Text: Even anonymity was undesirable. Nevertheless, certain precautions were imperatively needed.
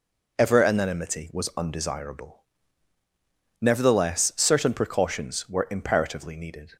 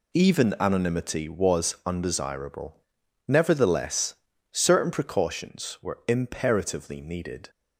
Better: second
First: says "Ever" for "Even"; at 0.3 s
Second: none

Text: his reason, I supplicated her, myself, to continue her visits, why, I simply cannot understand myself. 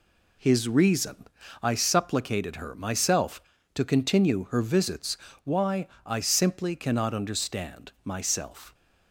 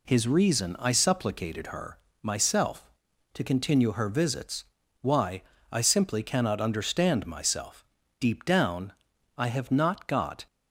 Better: first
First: none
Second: goes on to say "Deep down I have not got"; strong; from 8.2 s on; 2.2 s long

